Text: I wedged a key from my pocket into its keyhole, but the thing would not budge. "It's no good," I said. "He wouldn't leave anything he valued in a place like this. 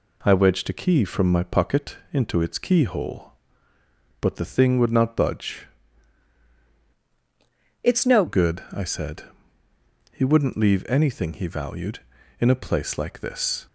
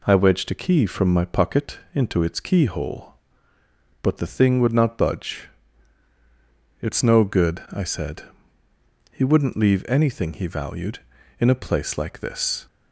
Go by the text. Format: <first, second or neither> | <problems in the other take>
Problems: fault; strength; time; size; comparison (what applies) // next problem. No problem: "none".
second | pauses between "pocket" and "into"; slight; at 1.9 s; 0.16 s long; slight in the second // changes voice from "It's" to "no"; from 7.8 to 8.2 s; 0.4 s long